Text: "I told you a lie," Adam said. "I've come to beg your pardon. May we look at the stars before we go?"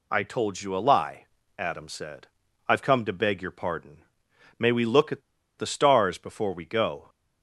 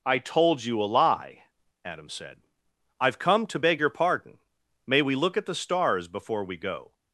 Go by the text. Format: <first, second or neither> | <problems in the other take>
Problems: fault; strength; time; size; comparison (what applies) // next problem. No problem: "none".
second | pauses between "at" and "the"; at 5.2 s; 0.37 s long